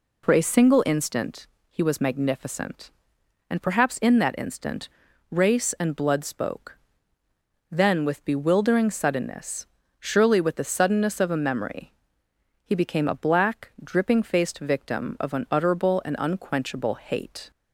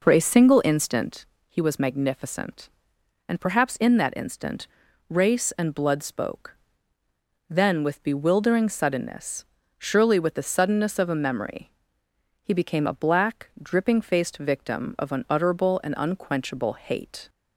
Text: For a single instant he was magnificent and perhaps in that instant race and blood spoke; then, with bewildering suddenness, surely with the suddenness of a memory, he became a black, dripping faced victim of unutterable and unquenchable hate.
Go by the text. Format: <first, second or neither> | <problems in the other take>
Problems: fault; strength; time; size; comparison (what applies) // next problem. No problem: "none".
first | starts louder than the rest; noticeable; until 1.4 s; 4.5 dB // pauses between "instant" and "he"; slight; at 1.2 s; 0.20 s long; slight in the first // pauses between "instant" and "race"; at 4.6 s; 0.42 s long; also in the first